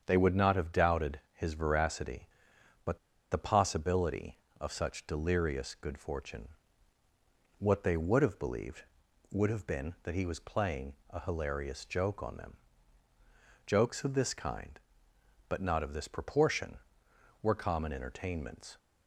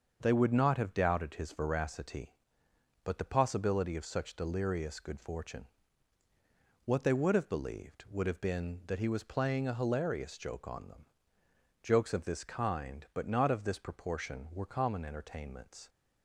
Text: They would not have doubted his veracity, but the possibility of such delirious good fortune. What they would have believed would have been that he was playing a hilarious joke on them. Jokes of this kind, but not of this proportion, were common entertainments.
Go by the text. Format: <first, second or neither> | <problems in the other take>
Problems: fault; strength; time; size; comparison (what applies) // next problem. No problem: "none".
second | starts louder than the rest; strong; until 1.0 s; 7.5 dB; also in the second // pauses between "but" and "the"; slight; at 2.9 s; 0.33 s long // pauses between "playing" and "a"; slight; at 10.9 s; 0.16 s long